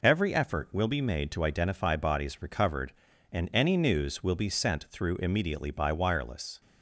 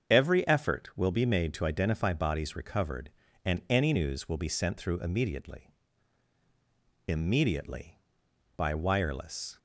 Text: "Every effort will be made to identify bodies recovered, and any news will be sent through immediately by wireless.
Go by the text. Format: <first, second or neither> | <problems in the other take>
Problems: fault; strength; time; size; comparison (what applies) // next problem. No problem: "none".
first | starts louder than the rest; strong; until 1.1 s; 7.5 dB // says "immediately" twice; at 7.0 s